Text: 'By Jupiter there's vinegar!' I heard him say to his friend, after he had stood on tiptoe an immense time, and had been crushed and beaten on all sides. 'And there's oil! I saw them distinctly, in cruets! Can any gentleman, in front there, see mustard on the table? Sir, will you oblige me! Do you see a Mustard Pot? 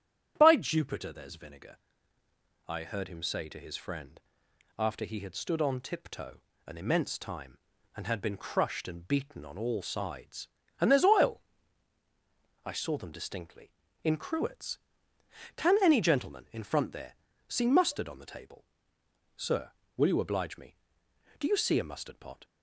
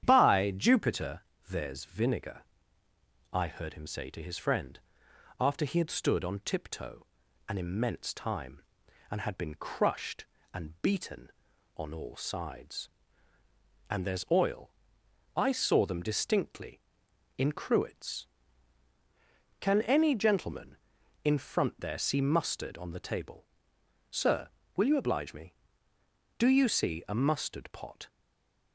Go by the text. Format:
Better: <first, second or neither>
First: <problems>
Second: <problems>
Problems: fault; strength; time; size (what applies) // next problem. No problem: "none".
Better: first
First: starts louder than the rest; strong; until 1.3 s; 10 dB // pauses between "tiptoe" and "an"; slight; at 6.4 s; 0.26 s long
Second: starts louder than the rest; strong; until 1.0 s; 9.5 dB // pauses between "Jupiter" and "there's"; slight; at 1.2 s; 0.30 s long // pauses between "tiptoe" and "an"; at 7.0 s; 0.42 s long // stays silent after the last word; slight; from 28.0 s on; 0.7 s long